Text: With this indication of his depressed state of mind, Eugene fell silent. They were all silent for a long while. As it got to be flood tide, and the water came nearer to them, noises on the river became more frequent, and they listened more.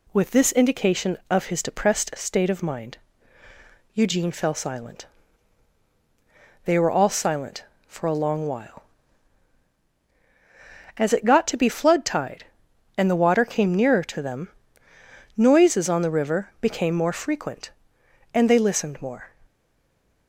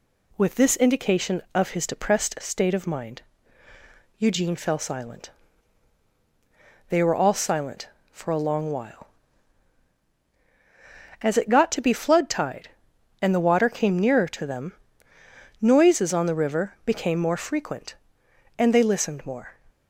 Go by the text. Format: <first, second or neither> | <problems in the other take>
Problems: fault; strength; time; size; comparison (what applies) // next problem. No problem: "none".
second | stays silent after the last word; slight; from 19.4 s on; 0.8 s long